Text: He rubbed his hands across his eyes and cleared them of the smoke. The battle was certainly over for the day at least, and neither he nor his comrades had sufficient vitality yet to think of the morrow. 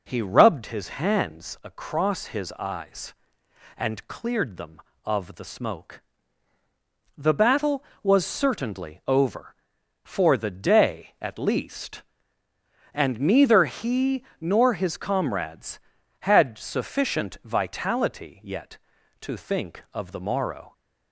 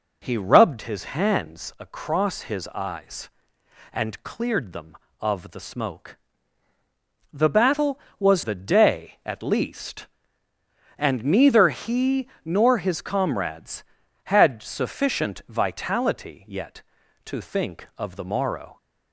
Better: first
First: pauses between "his" and "hands"; slight; at 0.8 s; 0.16 s long // pauses between "he" and "nor"; slight; at 14.2 s; 0.16 s long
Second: pauses between "his" and "hands"; slight; at 1.0 s; 0.16 s long // skips "certainly over for"; at 8.4 s // pauses between "he" and "nor"; slight; at 12.2 s; 0.16 s long

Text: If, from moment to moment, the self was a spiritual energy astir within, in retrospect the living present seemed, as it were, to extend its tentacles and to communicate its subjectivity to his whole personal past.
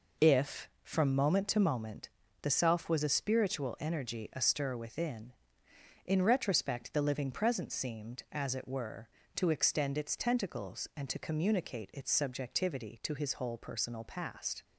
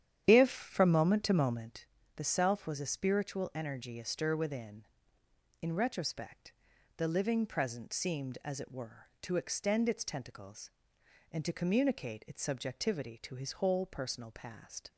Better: first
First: none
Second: starts louder than the rest; strong; until 1.8 s; 10 dB // pauses between "retrospect" and "the"; noticeable; at 6.5 s; 0.46 s long

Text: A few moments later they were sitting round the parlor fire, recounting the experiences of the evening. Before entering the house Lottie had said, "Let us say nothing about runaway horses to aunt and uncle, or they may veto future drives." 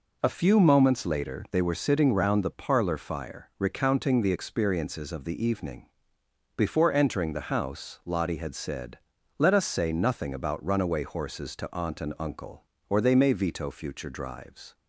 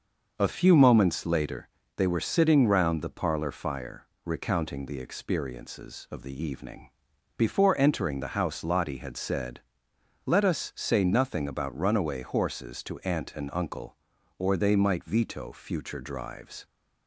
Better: first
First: none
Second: starts louder than the rest; noticeable; until 1.3 s; 6 dB // pauses between "later" and "they"; slight; at 1.6 s; 0.26 s long // says "might" for "may"; at 14.7 s

